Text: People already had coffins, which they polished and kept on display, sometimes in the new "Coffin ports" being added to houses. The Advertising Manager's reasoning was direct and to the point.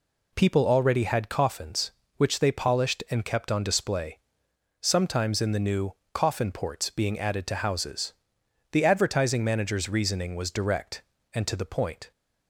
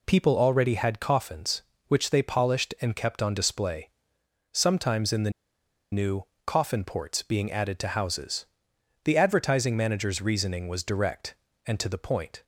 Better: first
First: pauses between "new" and "Coffin"; slight; at 5.9 s; 0.22 s long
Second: pauses between "the" and "new"; noticeable; at 5.3 s; 0.60 s long // pauses between "new" and "Coffin"; slight; at 6.2 s; 0.22 s long

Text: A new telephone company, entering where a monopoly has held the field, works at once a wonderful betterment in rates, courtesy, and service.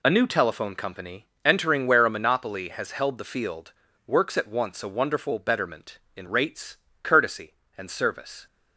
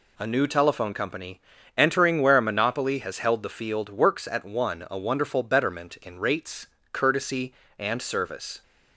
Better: first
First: none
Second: says "one" for "once"; at 4.4 s

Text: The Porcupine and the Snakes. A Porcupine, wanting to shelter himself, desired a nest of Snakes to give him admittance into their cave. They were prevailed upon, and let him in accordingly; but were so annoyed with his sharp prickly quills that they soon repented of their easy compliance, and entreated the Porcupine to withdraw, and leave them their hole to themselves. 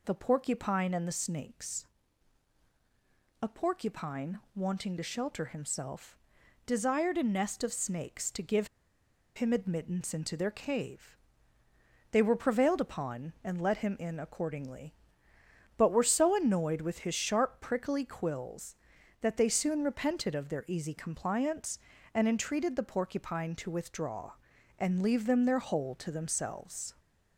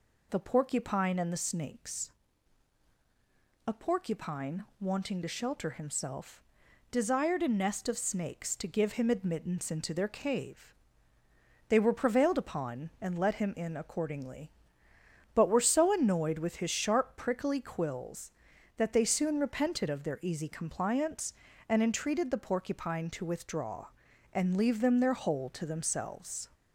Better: second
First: pauses between "give" and "him"; noticeable; at 8.6 s; 0.69 s long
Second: none

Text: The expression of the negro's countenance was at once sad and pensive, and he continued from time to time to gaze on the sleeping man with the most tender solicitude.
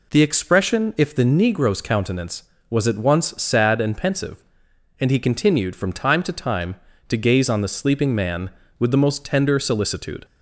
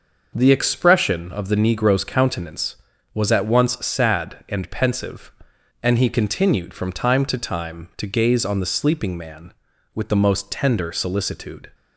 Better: second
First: says "if" for "of"; at 0.9 s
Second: none

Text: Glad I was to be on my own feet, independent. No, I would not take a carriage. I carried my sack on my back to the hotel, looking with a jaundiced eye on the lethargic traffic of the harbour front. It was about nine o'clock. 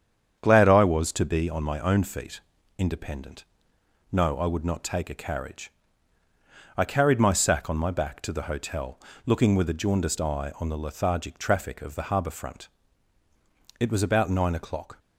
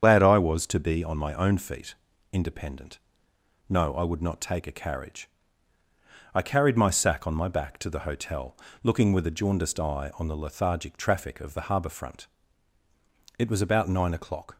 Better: first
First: starts louder than the rest; strong; until 1.4 s; 8 dB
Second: loses the start of "Glad"; at 0.0 s; 90 ms // starts louder than the rest; strong; until 1.0 s; 8 dB

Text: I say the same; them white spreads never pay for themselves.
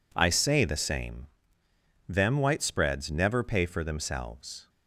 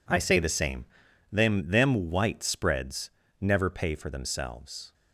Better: first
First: none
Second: says "them" twice; at 1.6 s // pauses between "spreads" and "never"; slight; at 3.0 s; 0.32 s long

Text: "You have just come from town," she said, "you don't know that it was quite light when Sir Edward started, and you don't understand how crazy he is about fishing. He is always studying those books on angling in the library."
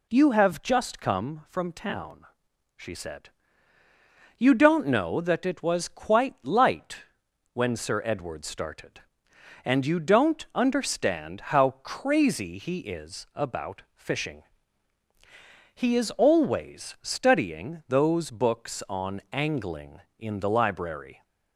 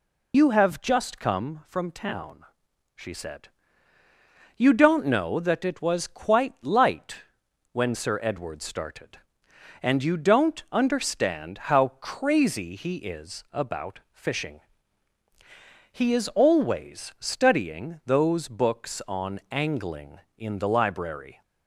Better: first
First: pauses between "light" and "when"; noticeable; at 7.0 s; 0.52 s long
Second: loses the start of "You"; at 0.3 s; 60 ms // pauses between "light" and "when"; noticeable; at 7.2 s; 0.52 s long

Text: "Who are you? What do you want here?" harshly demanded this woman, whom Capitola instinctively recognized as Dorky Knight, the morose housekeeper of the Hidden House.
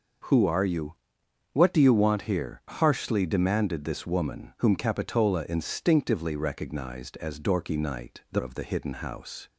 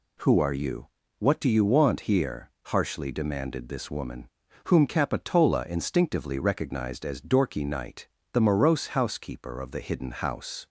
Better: second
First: skips "morose housekeeper"; at 8.3 s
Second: none

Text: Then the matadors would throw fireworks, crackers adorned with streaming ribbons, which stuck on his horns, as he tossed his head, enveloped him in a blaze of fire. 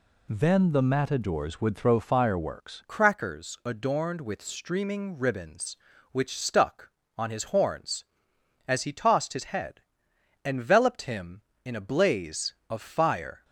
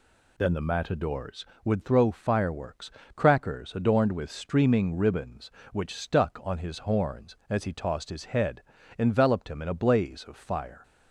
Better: second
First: changes voice at "crackers"; from 2.8 s on; 10.6 s long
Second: none

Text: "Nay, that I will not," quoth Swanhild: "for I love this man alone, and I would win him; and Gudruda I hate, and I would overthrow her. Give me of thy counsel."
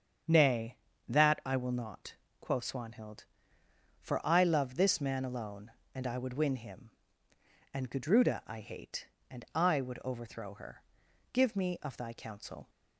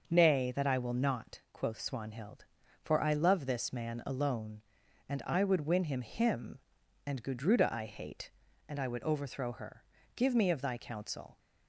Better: first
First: starts louder than the rest; strong; until 1.6 s; 7.5 dB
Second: starts louder than the rest; until 1.0 s; 6 dB // says "him" twice; at 6.0 s

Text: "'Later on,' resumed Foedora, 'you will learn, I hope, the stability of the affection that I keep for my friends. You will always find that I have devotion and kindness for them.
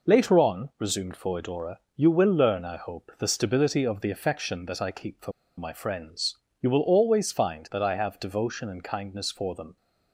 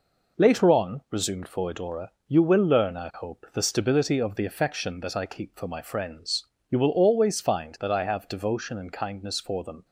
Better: second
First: pauses between "for" and "my"; slight; at 5.3 s; 0.26 s long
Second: none

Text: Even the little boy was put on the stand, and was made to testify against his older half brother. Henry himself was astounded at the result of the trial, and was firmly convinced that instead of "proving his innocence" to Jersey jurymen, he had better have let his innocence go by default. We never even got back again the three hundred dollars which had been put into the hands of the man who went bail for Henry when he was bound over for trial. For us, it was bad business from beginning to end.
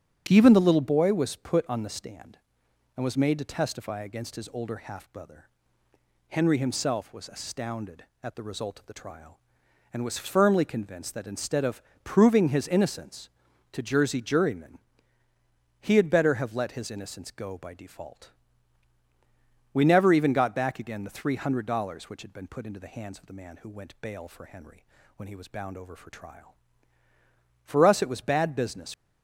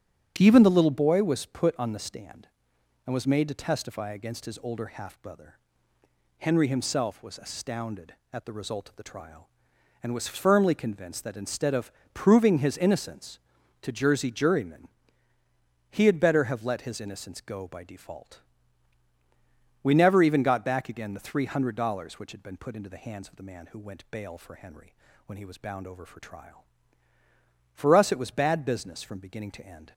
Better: second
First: starts louder than the rest; strong; until 1.2 s; 8.5 dB // pauses between "of" and "proving"; slight; at 11.8 s; 0.22 s long // pauses between "Henry" and "when"; slight; at 24.8 s; 0.32 s long // stops before "from beginning to end"; at 28.9 s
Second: starts louder than the rest; strong; until 1.3 s; 8 dB // pauses between "of" and "proving"; slight; at 11.9 s; 0.22 s long // pauses between "Henry" and "when"; slight; at 24.9 s; 0.32 s long

